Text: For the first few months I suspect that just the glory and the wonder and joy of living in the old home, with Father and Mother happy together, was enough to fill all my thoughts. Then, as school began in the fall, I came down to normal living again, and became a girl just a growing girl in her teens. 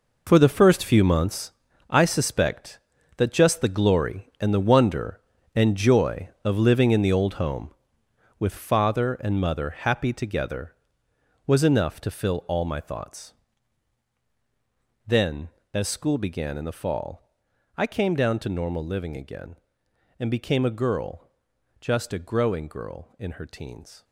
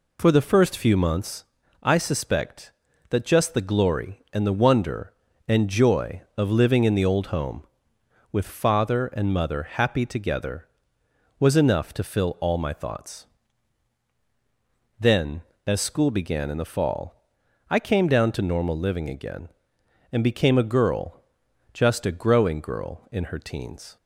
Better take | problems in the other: second | gets quieter; strong; throughout; 12 dB // pauses between "months" and "I"; slight; at 1.5 s; 0.36 s long; slight in the second // pauses between "girl" and "just"; noticeable; at 21.2 s; 0.50 s long; noticeable in the second

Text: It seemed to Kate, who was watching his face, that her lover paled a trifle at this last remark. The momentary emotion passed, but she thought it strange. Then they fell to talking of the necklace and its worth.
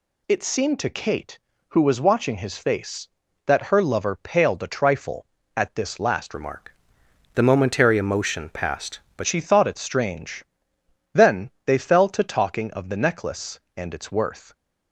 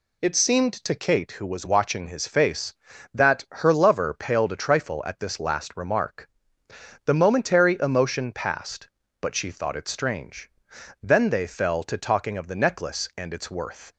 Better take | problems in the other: second | changes voice from "remark" to "but"; from 6.3 to 9.2 s; 2.9 s long

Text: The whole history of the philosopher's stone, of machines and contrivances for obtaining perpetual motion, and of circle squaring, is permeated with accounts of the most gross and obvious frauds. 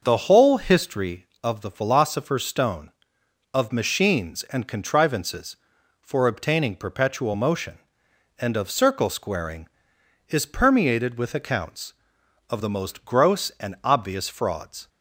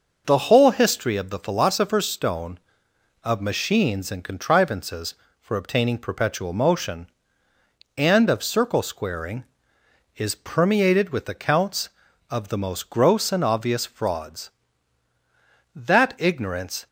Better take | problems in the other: first | starts louder than the rest; noticeable; until 1.2 s; 6 dB; noticeable in the first // goes on to say "That ignorance"; noticeable; from 15.7 s on; 1.1 s long

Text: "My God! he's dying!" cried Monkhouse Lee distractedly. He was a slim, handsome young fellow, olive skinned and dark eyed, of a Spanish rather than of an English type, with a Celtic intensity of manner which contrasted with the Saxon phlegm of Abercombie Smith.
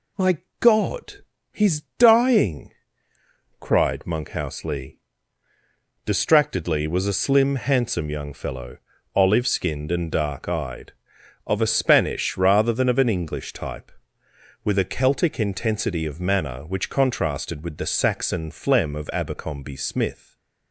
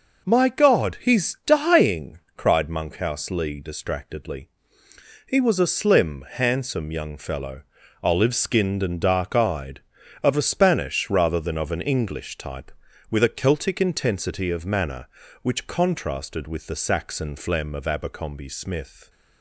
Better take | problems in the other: second | pauses between "My" and "God"; slight; at 0.3 s; 0.22 s long // pauses between "he's" and "dying"; slight; at 1.7 s; 0.18 s long // pauses between "Lee" and "distractedly"; at 4.9 s; 1.0 s long // skips "He"; at 6.8 s // stays silent after the last word; slight; from 20.1 s on; 0.6 s long

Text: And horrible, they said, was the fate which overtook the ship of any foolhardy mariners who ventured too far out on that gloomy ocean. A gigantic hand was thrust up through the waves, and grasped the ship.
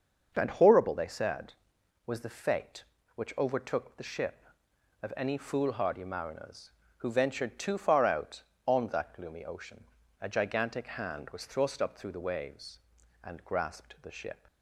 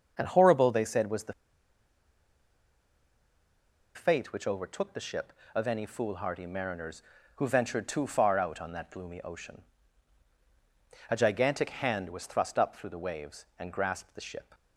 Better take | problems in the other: first | starts louder than the rest; until 1.1 s; 6.5 dB; also in the first // pauses between "the" and "fate"; strong; at 1.3 s; 2.6 s long

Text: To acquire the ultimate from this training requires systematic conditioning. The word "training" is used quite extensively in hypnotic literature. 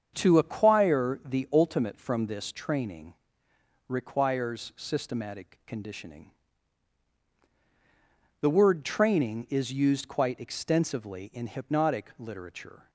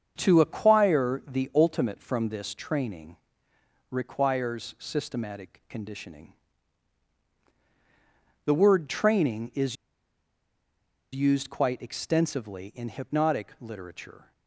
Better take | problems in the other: first | starts louder than the rest; strong; until 1.1 s; 7 dB; strong in the first // pauses between "training" and "requires"; noticeable; at 3.1 s; 0.74 s long; noticeable in the first // pauses between "is" and "used"; strong; at 9.7 s; 1.3 s long

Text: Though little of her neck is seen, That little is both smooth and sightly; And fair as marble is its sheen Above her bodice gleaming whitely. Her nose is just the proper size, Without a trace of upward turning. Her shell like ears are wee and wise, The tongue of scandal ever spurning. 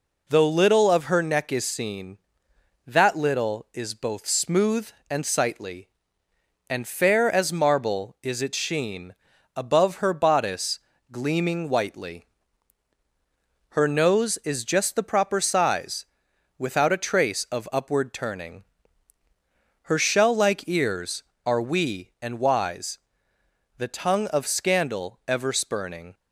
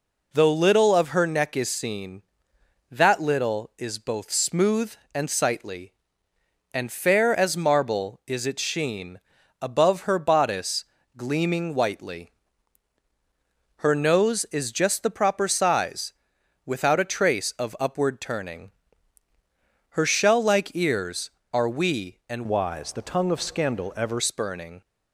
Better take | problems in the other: first | pauses between "sheen" and "Above"; at 9.1 s; 0.42 s long; also in the first // pauses between "bodice" and "gleaming"; slight; at 10.8 s; 0.32 s long; slight in the first // changes voice from "wise" to "ever"; from 22.4 to 24.2 s; 1.8 s long

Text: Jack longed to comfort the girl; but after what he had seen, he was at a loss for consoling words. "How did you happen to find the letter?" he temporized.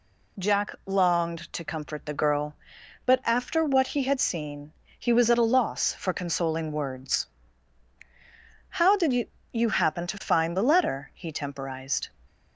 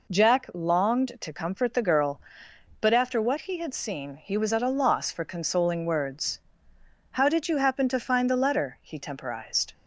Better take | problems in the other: second | says "you" twice; at 9.5 s

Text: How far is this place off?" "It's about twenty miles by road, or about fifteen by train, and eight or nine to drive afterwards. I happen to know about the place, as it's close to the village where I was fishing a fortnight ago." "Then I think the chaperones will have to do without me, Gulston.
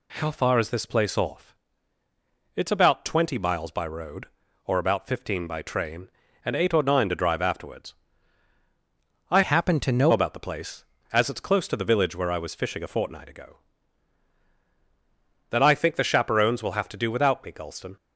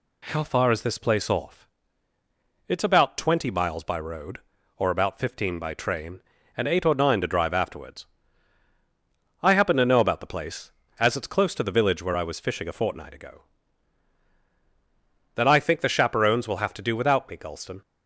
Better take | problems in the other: second | changes voice from "happen" to "know"; from 9.4 to 10.1 s; 0.7 s long

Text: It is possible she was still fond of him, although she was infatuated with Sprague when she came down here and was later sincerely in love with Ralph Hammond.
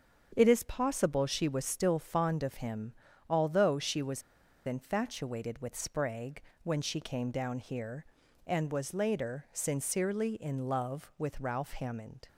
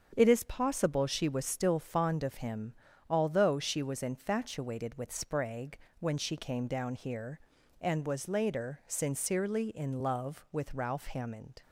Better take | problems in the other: second | starts louder than the rest; strong; until 1.3 s; 7.5 dB; strong in the second // pauses between "was" and "infatuated"; at 4.2 s; 0.45 s long // pauses between "Sprague" and "when"; slight; at 6.3 s; 0.22 s long; slight in the second

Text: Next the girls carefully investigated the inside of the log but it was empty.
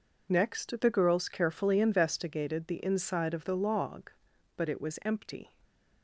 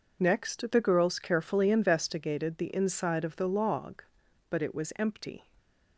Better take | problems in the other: neither | none

